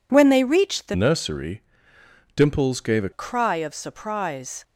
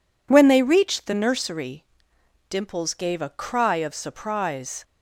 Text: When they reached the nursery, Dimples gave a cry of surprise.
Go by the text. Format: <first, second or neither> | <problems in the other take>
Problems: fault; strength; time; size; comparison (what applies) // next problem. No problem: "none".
second | changes voice from "nursery" to "a"; from 0.9 to 3.0 s; 2.1 s long